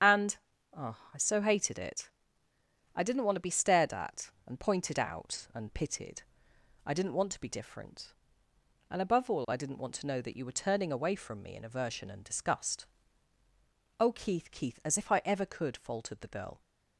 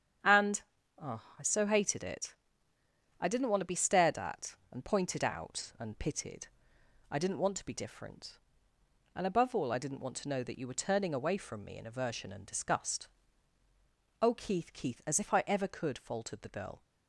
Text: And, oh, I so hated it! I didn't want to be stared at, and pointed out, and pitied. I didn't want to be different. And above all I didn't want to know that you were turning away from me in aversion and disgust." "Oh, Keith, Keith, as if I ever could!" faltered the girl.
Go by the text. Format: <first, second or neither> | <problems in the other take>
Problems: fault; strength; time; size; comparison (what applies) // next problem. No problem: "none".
second | loses the start of "And"; at 0.0 s; 40 ms // starts louder than the rest; strong; until 1.6 s; 8 dB; strong in the second